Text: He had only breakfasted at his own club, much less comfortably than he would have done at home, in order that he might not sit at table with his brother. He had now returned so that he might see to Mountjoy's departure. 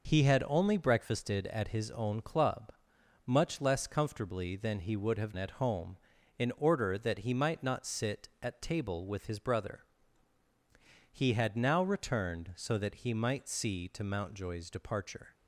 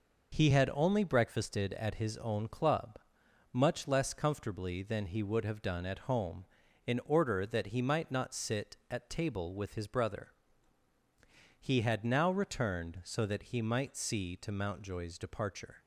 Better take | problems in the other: second | skips "done"; at 5.3 s

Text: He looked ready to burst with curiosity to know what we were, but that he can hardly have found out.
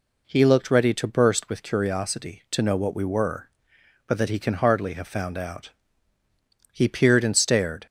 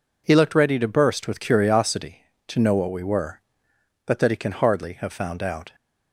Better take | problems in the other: second | goes on to say "He peered and stared"; noticeable; from 6.7 s on; 1.1 s long

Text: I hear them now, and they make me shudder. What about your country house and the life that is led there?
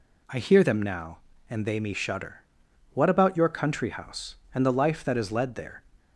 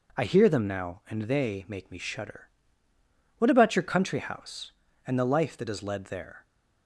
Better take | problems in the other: second | skips "make"; at 1.7 s

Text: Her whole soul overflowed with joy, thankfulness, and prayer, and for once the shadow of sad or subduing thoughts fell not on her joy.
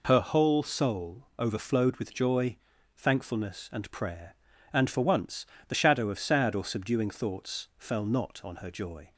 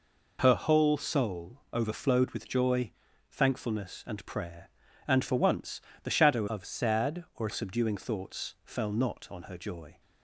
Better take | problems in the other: first | pauses between "once" and "the"; slight; at 5.8 s; 0.20 s long; slight in the first // changes voice from "of" to "or"; from 6.4 to 7.4 s; 1.0 s long

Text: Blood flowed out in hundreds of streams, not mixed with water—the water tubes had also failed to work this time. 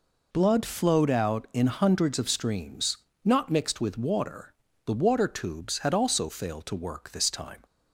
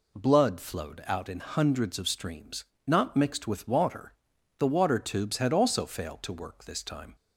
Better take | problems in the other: neither | none

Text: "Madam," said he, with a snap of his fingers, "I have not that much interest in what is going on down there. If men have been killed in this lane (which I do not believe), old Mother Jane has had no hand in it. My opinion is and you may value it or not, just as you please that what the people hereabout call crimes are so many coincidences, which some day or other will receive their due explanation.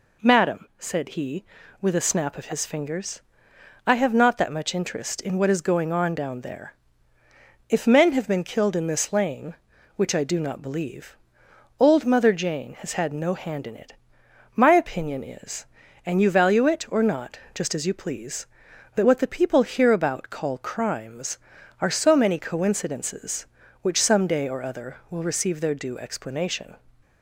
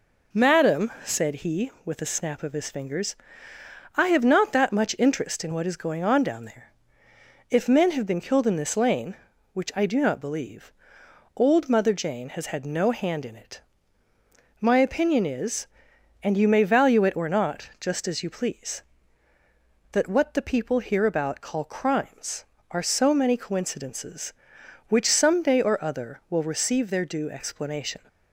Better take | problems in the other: second | skips "may"; at 16.3 s

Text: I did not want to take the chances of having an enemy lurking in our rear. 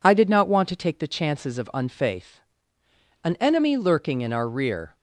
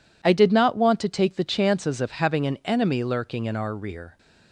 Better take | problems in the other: second | says "unfaith" for "having"; at 1.7 s

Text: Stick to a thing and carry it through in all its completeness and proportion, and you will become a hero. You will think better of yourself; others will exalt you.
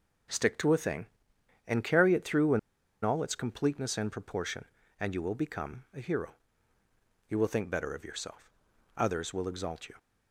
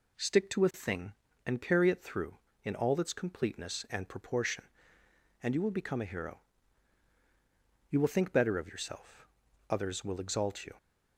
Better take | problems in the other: second | pauses between "in" and "all"; at 2.5 s; 0.44 s long

